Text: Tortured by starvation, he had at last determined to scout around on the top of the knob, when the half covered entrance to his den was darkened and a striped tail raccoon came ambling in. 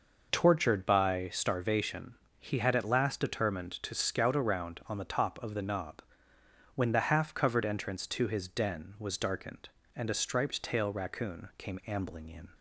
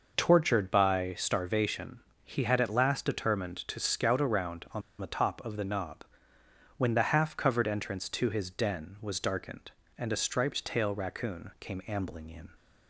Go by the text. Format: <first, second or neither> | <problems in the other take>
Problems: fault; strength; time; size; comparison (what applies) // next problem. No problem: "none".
first | pauses between "on" and "the"; slight; at 4.8 s; 0.17 s long